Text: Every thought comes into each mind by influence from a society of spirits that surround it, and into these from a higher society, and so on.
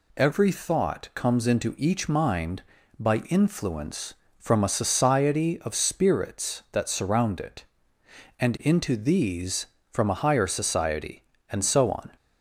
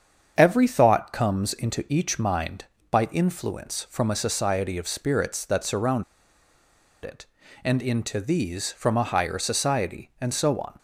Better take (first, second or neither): first